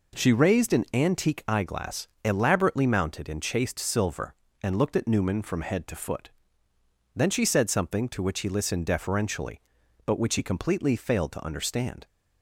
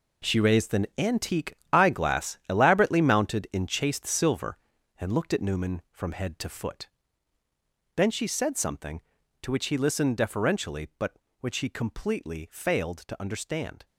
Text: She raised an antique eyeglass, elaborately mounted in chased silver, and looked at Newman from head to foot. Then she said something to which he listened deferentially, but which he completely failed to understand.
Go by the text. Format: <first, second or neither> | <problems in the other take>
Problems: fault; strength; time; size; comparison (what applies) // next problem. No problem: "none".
first | gets quieter; strong; throughout; 11 dB // pauses between "antique" and "eyeglass"; slight; at 1.5 s; 0.20 s long